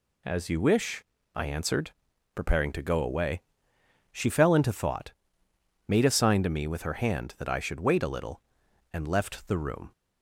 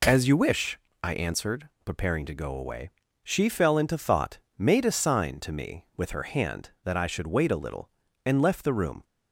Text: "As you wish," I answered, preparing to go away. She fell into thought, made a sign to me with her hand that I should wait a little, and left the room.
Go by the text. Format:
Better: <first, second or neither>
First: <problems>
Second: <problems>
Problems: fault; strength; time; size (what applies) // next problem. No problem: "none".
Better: neither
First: none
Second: none